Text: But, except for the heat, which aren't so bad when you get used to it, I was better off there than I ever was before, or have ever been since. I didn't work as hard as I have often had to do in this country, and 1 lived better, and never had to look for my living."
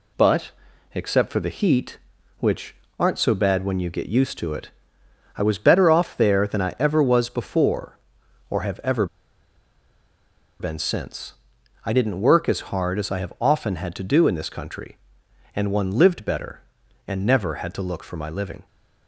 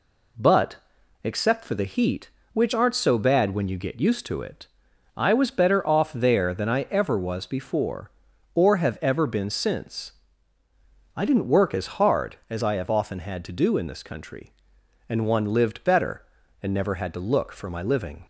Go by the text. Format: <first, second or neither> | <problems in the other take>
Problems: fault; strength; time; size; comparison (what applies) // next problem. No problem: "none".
second | pauses between "which" and "aren't"; slight; at 2.7 s; 0.26 s long // pauses between "ever" and "been"; strong; at 9.0 s; 1.5 s long